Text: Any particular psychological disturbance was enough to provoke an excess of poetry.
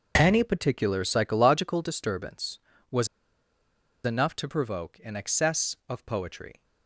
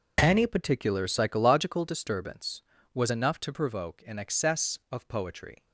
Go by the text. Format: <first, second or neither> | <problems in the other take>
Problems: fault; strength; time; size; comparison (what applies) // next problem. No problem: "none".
second | pauses between "was" and "enough"; at 3.0 s; 0.98 s long